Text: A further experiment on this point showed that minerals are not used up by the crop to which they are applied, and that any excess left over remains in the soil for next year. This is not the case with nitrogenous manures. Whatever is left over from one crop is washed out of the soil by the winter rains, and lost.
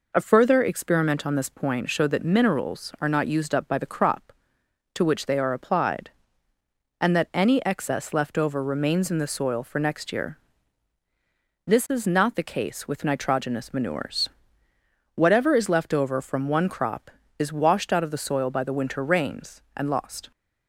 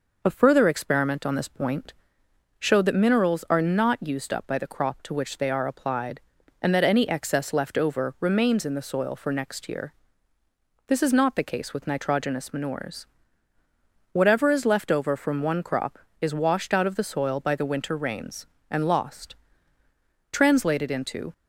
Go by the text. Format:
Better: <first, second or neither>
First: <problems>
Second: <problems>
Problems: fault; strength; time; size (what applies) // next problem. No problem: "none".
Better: first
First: none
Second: pauses between "point" and "showed"; noticeable; at 1.9 s; 0.64 s long // goes on to say "Translated into"; noticeable; from 20.3 s on; 1.0 s long